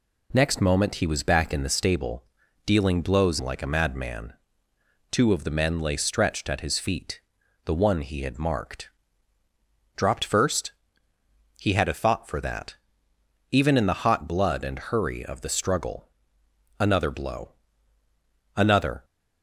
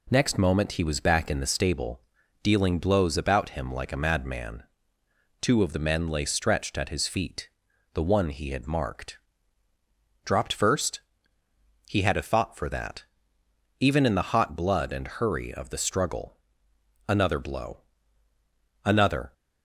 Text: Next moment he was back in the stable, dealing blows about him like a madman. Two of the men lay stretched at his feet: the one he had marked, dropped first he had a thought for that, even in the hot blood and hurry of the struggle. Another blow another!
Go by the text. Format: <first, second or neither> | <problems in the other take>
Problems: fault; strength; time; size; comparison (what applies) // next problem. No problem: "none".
second | skips "about him"; at 3.4 s // pauses between "first" and "he"; noticeable; at 10.7 s; 0.88 s long; noticeable in the second // pauses between "blow" and "another"; at 17.5 s; 1.0 s long; also in the second